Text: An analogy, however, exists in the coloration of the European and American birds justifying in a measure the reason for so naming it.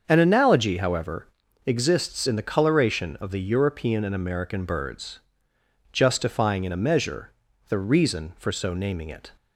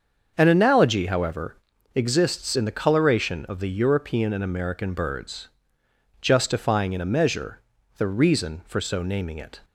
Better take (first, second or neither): neither